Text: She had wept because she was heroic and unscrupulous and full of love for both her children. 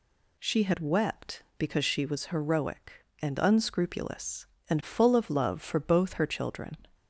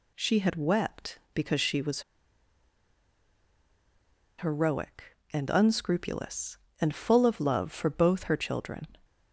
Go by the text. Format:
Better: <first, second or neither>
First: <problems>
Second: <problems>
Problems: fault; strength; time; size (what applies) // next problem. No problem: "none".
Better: first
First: none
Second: pauses between "was" and "heroic"; strong; at 2.0 s; 2.3 s long